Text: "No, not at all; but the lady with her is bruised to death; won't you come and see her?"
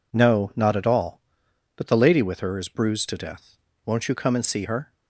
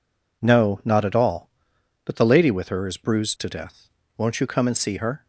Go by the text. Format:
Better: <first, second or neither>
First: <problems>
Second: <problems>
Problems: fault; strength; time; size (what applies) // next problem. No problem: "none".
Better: neither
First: none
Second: none